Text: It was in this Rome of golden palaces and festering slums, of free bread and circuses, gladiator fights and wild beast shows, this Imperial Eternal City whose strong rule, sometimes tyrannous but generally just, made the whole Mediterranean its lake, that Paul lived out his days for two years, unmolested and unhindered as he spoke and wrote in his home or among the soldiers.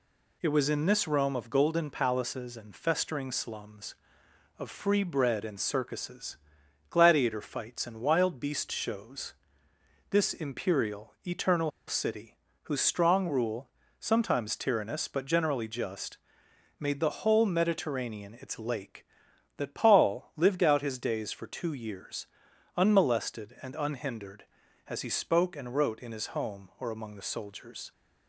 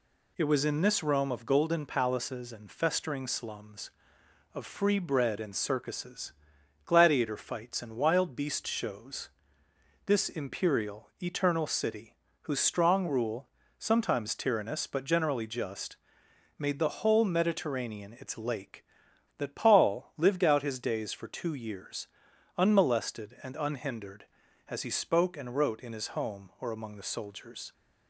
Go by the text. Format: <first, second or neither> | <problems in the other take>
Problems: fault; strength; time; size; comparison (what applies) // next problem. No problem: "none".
second | pauses between "Eternal" and "City"; slight; at 11.7 s; 0.17 s long // pauses between "City" and "whose"; slight; at 12.3 s; 0.28 s long; slight in the second